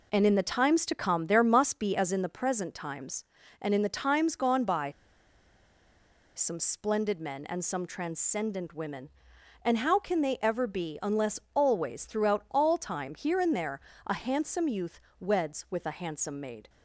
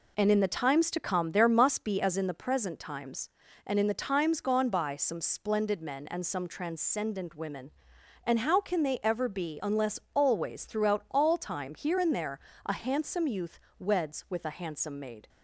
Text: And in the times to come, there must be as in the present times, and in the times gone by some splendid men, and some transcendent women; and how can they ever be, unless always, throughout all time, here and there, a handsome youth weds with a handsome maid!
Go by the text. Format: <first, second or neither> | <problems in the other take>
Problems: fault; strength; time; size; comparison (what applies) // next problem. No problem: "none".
second | pauses between "by" and "some"; strong; at 4.8 s; 1.4 s long // pauses between "youth" and "weds"; slight; at 15.0 s; 0.18 s long; slight in the second